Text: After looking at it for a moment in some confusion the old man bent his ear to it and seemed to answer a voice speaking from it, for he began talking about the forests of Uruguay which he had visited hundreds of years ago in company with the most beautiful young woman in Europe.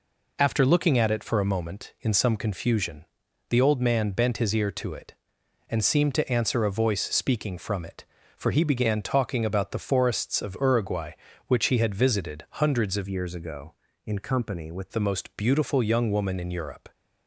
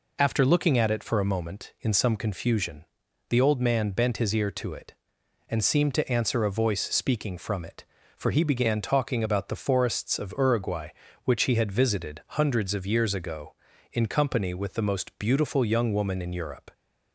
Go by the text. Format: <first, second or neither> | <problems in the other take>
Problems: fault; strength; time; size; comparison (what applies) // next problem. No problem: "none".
second | pauses between "confusion" and "the"; at 3.0 s; 0.44 s long; also in the second // changes voice from "years" to "with"; from 13.0 to 14.8 s; 1.8 s long